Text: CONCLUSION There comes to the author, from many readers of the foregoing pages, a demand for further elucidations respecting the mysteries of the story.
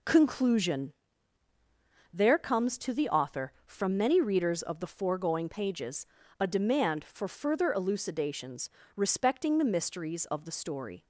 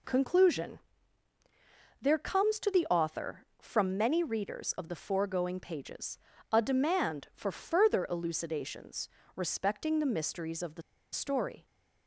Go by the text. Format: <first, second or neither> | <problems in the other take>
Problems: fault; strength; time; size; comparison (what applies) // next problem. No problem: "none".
first | pauses between "CONCLUSION" and "There"; at 0.7 s; 1.2 s long; also in the first // pauses between "elucidations" and "respecting"; slight; at 9.0 s; 0.26 s long; slight in the first // pauses between "the" and "story"; slight; at 10.8 s; 0.31 s long